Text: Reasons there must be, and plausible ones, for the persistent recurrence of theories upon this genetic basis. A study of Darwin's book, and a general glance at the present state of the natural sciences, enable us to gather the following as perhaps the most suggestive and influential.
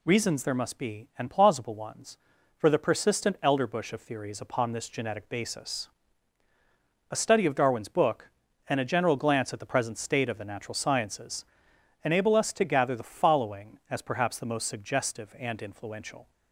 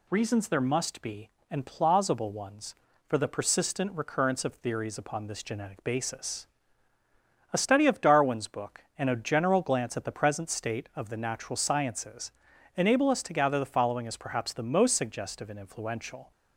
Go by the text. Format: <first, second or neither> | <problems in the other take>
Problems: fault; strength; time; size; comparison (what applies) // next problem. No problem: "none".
second | says "elderbush" for "recurrence"; at 3.4 s